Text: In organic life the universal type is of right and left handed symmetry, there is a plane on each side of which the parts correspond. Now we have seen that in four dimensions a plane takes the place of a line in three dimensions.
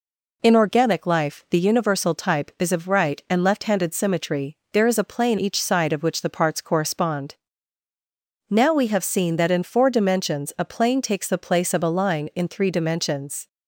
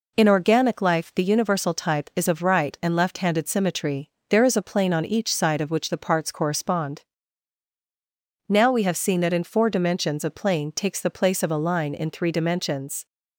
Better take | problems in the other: second | skips "on"; at 5.3 s

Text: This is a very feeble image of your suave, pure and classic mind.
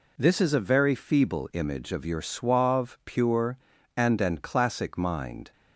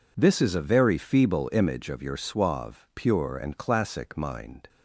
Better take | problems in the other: second | says "and" twice; at 4.2 s

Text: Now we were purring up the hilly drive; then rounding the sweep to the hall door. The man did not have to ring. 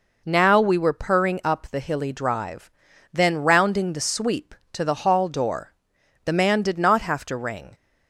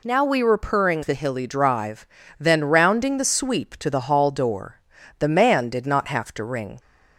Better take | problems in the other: first | skips "up"; at 1.0 s

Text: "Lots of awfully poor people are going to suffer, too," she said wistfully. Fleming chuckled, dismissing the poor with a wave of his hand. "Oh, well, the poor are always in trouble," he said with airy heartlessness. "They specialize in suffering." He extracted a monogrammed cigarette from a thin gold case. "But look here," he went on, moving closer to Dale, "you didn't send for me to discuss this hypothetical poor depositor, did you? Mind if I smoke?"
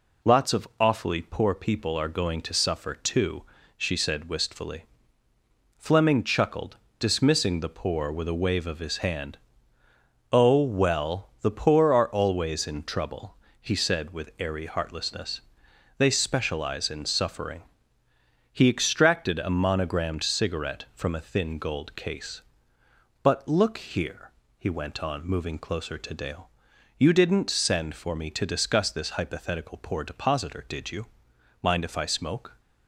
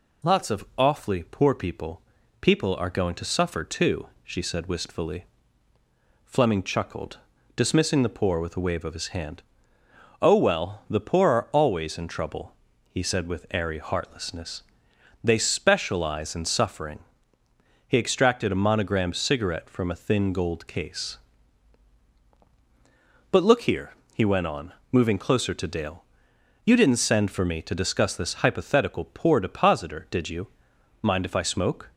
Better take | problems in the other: first | says "people" twice; at 2.3 s

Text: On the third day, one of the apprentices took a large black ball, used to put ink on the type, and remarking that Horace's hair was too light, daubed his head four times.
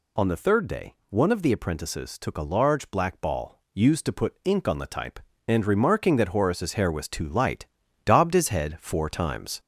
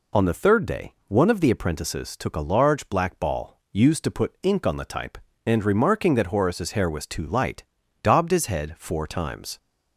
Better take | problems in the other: second | gets louder; noticeable; throughout; 4 dB

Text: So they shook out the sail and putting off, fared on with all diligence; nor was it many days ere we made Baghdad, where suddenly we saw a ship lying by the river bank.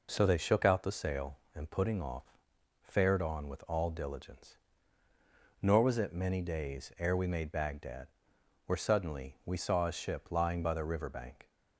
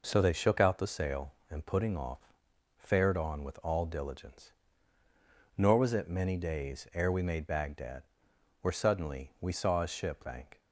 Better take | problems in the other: first | skips "lying by the river"; at 10.2 s

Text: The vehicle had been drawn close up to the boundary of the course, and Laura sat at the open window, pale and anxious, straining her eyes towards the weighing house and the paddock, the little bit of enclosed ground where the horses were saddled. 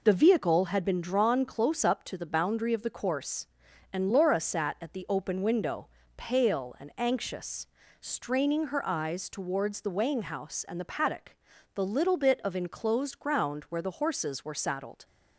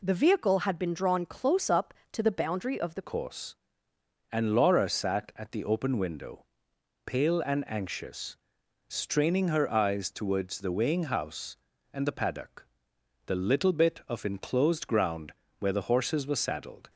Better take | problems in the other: first | changes voice at "course"; from 3.0 s on; 13.8 s long // pauses between "ground" and "where"; slight; at 15.3 s; 0.28 s long

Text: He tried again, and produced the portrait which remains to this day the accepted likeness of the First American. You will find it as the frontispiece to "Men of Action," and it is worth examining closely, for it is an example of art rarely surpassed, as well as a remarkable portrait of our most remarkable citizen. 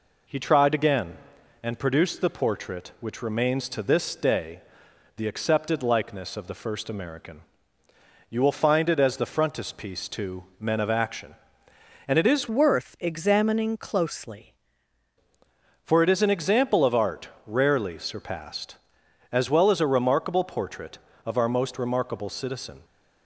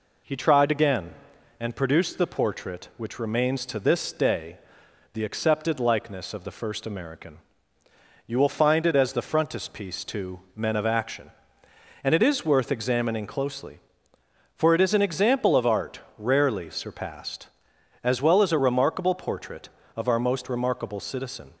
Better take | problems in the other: second | pauses between "day" and "the"; noticeable; at 4.6 s; 0.56 s long; noticeable in the second // pauses between "to" and "Men"; slight; at 10.4 s; 0.16 s long; slight in the second // changes voice from "worth" to "closely"; from 12.5 to 14.5 s; 2.0 s long // pauses between "art" and "rarely"; slight; at 17.2 s; 0.16 s long; slight in the second

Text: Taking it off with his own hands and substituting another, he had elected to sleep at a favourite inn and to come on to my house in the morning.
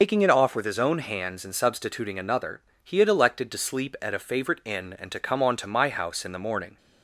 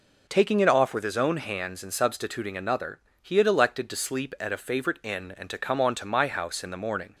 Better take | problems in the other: second | loses the start of "Taking"; at 0.0 s; 100 ms

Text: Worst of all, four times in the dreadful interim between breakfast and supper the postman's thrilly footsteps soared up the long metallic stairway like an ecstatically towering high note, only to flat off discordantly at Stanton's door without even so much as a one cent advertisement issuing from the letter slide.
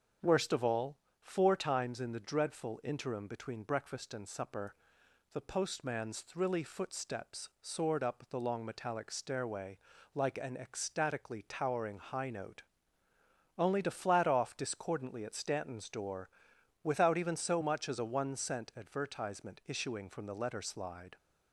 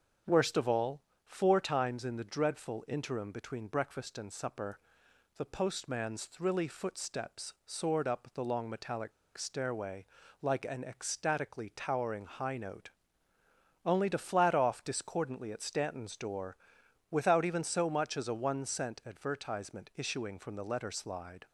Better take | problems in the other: first | starts louder than the rest; strong; until 1.5 s; 7 dB; strong in the first // pauses between "supper" and "the"; noticeable; at 4.7 s; 0.60 s long; noticeable in the first // pauses between "metallic" and "stairway"; slight; at 9.1 s; 0.25 s long // pauses between "stairway" and "like"; at 10.0 s; 0.38 s long; also in the first // pauses between "door" and "without"; noticeable; at 16.5 s; 0.52 s long; noticeable in the first

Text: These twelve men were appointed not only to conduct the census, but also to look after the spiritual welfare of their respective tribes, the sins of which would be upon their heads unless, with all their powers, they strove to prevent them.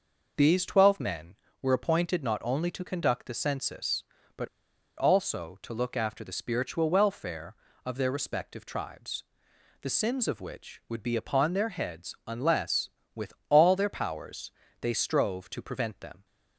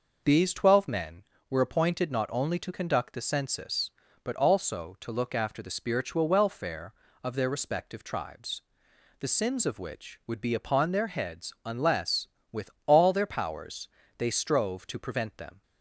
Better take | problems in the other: second | pauses between "but" and "also"; noticeable; at 4.4 s; 0.50 s long // pauses between "with" and "all"; slight; at 13.3 s; 0.16 s long; slight in the second

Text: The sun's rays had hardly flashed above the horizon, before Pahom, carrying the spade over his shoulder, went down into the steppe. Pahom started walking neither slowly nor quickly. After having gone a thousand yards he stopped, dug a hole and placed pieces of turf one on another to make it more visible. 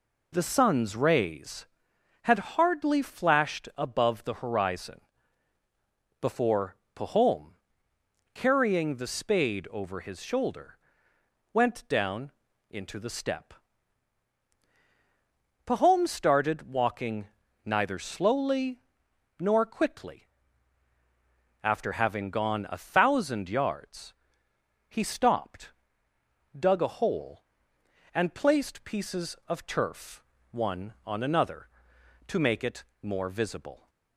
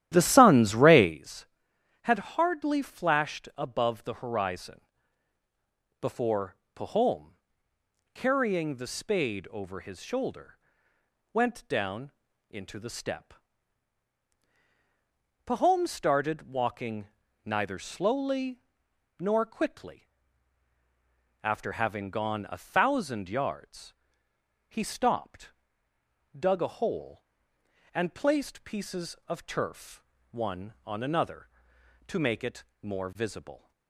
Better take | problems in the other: first | starts louder than the rest; strong; until 1.2 s; 12.5 dB // pauses between "before" and "Pahom"; slight; at 6.5 s; 0.18 s long; slight in the first // pauses between "down" and "into"; at 12.1 s; 0.40 s long; also in the first // pauses between "walking" and "neither"; slight; at 17.0 s; 0.36 s long; slight in the first // pauses between "slowly" and "nor"; noticeable; at 18.5 s; 0.60 s long; noticeable in the first // pauses between "yards" and "he"; noticeable; at 23.9 s; 0.74 s long; noticeable in the first // pauses between "turf" and "one"; slight; at 30.0 s; 0.30 s long; slight in the first // pauses between "it" and "more"; slight; at 32.6 s; 0.16 s long; slight in the first

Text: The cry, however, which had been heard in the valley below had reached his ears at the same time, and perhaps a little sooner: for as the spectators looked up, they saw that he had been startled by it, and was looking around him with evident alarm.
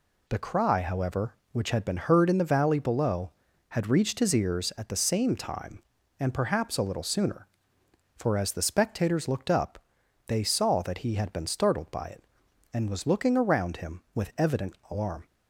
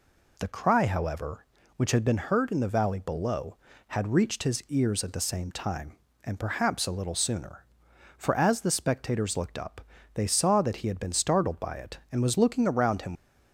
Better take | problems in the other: first | stops before "with evident alarm"; at 13.1 s

